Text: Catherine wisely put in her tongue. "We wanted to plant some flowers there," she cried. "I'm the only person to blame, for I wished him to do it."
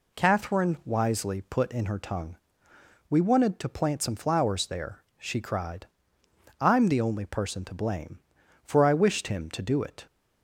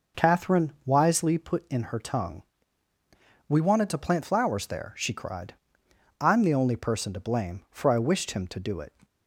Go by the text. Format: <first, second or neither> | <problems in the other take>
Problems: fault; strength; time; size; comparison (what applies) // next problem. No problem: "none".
first | skips "some"; at 4.2 s